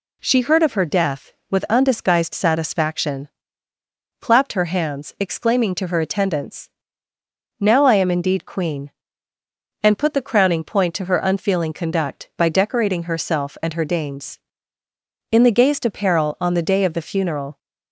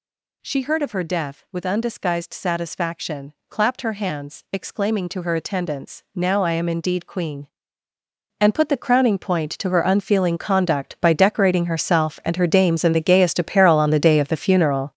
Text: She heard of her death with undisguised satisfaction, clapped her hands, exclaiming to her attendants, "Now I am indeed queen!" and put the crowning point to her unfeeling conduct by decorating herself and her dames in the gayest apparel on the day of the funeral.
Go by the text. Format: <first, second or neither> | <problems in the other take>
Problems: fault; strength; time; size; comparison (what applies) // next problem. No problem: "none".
first | gets louder; strong; throughout; 11 dB